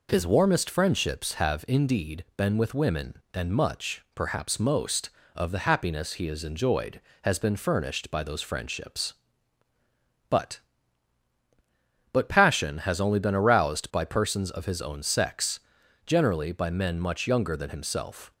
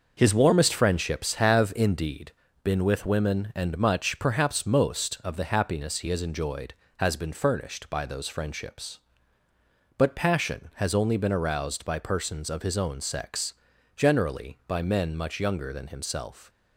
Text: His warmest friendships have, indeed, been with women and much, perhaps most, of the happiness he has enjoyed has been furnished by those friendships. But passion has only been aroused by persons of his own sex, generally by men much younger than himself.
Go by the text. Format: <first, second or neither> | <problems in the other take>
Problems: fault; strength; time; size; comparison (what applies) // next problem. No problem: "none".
second | says "But" twice; at 12.1 s